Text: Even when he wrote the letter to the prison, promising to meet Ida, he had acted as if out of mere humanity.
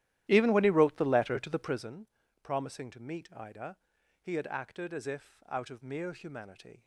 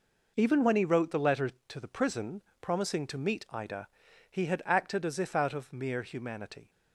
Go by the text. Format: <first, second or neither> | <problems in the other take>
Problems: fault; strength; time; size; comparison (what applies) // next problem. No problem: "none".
second | starts louder than the rest; strong; until 2.0 s; 13.5 dB